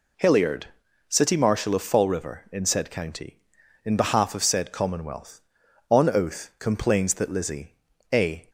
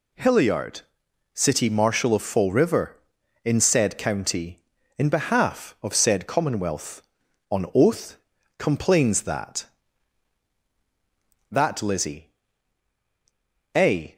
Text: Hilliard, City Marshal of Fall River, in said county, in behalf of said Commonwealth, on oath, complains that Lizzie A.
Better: first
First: pauses between "Lizzie" and "A"; at 7.7 s; 0.40 s long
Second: says "that" twice; at 11.5 s // pauses between "Lizzie" and "A"; strong; at 12.2 s; 1.4 s long

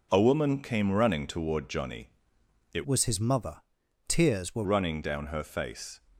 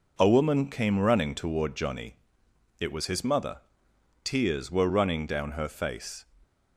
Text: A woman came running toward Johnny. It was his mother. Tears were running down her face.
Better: second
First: changes voice from "was" to "were"; from 2.8 to 4.6 s; 1.8 s long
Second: none

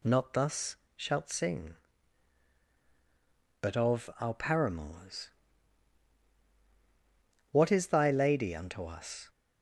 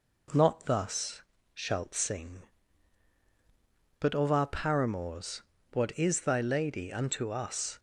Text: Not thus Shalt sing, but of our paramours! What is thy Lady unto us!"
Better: neither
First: pauses between "thus" and "Shalt"; slight; at 0.7 s; 0.22 s long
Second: pauses between "thus" and "Shalt"; slight; at 1.2 s; 0.32 s long

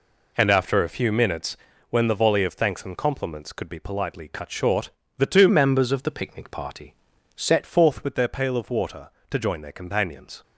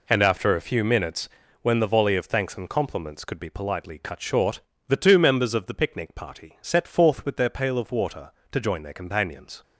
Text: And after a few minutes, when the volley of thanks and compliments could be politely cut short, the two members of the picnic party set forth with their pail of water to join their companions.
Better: second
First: changes voice from "members" to "set"; from 5.4 to 7.6 s; 2.2 s long // pauses between "party" and "set"; at 6.9 s; 0.42 s long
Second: none

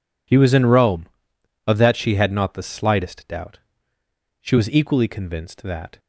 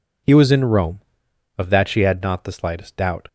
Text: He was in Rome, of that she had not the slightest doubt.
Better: second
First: goes on to say "She was equally convinced that"; from 4.4 s on; 1.5 s long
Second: none

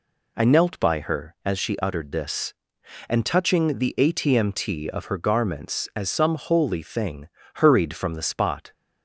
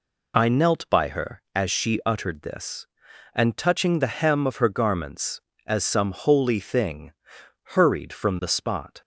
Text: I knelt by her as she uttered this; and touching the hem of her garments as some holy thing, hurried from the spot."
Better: second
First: says "atmt" for "hem"; at 3.9 s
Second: none

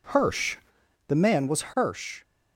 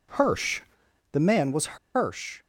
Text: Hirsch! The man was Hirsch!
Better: first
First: none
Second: pauses between "was" and "Hirsch"; slight; at 1.7 s; 0.17 s long

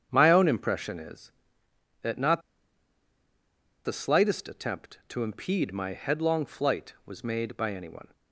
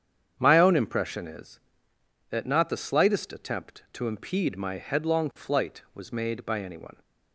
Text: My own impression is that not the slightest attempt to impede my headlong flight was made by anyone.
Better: second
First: starts louder than the rest; strong; until 1.1 s; 8 dB // pauses between "not" and "the"; strong; at 2.4 s; 1.4 s long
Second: starts louder than the rest; strong; until 1.4 s; 8 dB

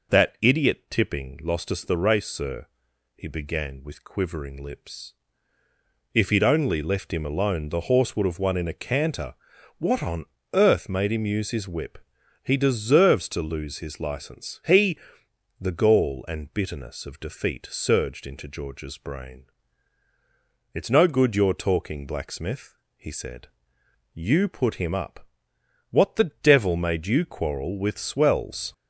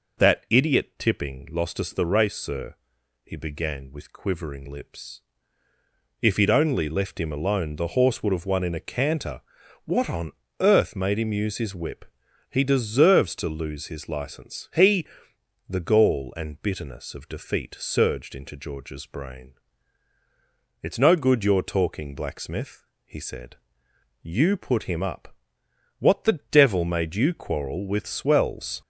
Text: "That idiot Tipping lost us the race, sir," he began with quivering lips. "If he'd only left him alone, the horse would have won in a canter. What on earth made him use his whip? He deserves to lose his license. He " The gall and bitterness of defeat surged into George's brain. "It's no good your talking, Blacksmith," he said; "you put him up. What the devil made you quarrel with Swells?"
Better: neither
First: pauses between "on" and "earth"; slight; at 10.2 s; 0.28 s long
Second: pauses between "on" and "earth"; slight; at 10.3 s; 0.28 s long

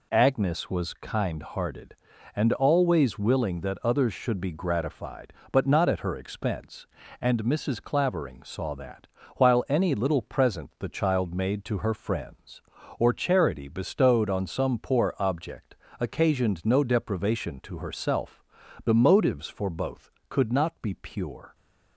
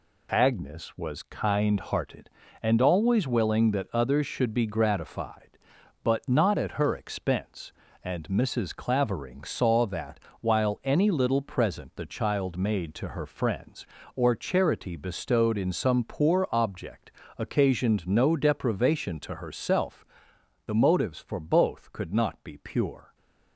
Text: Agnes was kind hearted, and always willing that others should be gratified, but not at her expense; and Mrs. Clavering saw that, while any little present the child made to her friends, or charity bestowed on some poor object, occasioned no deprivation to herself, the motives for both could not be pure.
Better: first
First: none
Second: says "in" for "on"; at 15.5 s

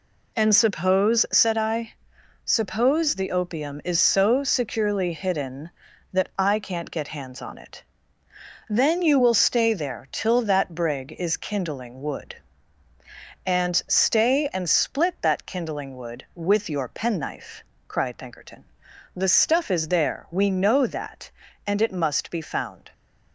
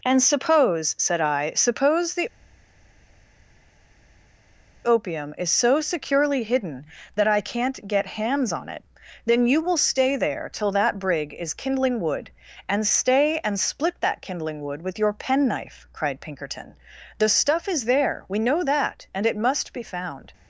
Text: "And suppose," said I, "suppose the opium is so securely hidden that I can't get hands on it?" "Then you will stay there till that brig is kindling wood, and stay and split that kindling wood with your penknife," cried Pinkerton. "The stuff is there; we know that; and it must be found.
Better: first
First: none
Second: pauses between "the" and "opium"; strong; at 2.2 s; 2.5 s long

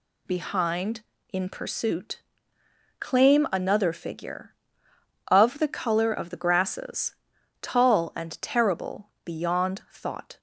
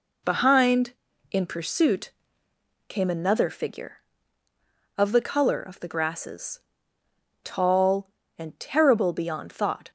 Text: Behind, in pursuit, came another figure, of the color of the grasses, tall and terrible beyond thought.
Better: second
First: says "claim" for "came"; at 2.9 s // pauses between "terrible" and "beyond"; slight; at 9.0 s; 0.16 s long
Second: none

